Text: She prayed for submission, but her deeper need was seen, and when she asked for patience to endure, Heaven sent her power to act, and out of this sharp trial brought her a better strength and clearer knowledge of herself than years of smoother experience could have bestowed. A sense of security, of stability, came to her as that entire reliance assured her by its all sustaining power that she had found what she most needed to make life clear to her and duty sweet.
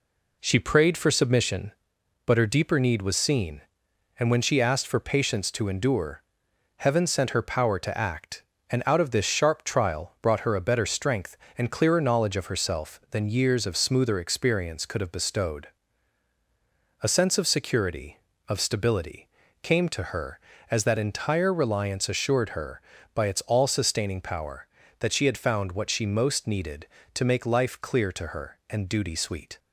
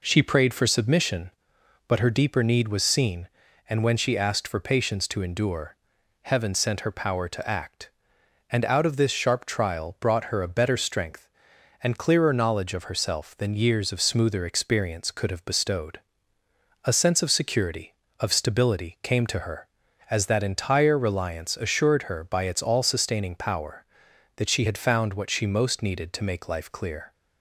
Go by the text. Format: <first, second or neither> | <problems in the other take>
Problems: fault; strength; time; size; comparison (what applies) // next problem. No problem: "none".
first | stops before "to her and duty sweet"; at 27.1 s